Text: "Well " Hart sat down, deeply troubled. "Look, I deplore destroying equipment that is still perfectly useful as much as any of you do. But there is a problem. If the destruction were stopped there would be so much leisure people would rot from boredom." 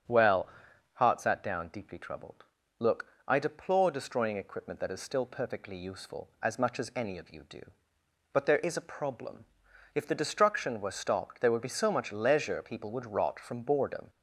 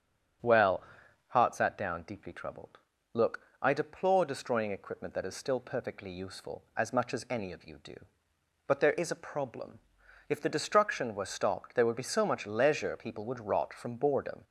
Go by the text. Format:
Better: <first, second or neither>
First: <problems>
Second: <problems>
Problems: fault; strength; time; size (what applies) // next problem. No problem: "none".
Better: neither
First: starts louder than the rest; strong; until 1.3 s; 8.5 dB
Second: starts louder than the rest; strong; until 1.6 s; 8.5 dB